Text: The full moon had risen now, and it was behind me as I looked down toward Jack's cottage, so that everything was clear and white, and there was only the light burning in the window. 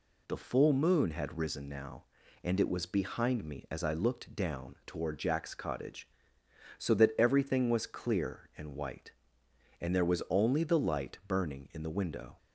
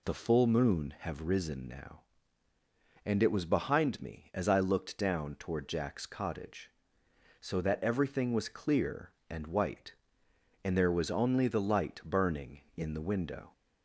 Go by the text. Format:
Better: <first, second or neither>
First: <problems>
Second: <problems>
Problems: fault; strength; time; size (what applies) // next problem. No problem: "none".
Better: first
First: none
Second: says "have" for "had"; at 0.9 s